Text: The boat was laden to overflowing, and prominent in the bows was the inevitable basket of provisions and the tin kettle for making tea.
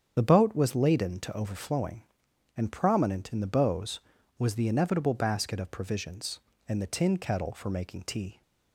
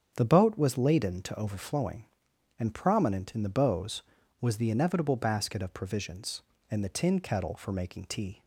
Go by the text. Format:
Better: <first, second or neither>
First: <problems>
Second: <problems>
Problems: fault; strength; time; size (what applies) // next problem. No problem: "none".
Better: second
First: loses the start of "The"; at 0.1 s; 40 ms // starts louder than the rest; strong; until 1.1 s; 8 dB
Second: starts louder than the rest; strong; until 1.1 s; 8 dB